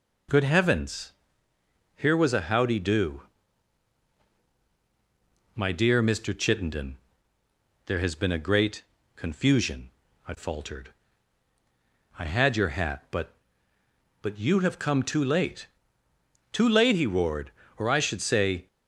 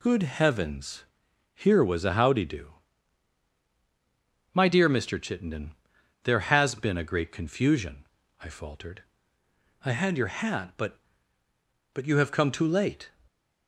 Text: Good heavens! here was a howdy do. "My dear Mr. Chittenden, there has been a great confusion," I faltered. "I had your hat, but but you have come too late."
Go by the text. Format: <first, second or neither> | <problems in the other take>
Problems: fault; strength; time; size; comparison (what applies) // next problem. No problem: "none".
second | pauses between "great" and "confusion"; slight; at 8.8 s; 0.32 s long // goes on to say "Too late he roared or I should say"; strong; from 16.5 s on; 2.1 s long